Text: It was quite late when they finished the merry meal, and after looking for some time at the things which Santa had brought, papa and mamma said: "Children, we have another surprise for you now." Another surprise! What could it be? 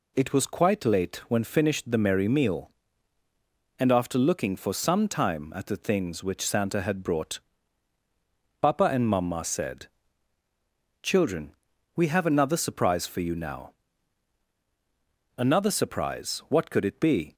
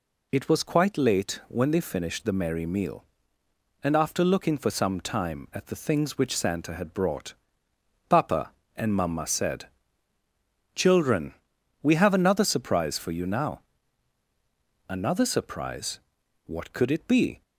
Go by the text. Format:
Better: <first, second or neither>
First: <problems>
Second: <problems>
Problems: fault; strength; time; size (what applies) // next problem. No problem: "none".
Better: second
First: skips "they"; at 1.4 s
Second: none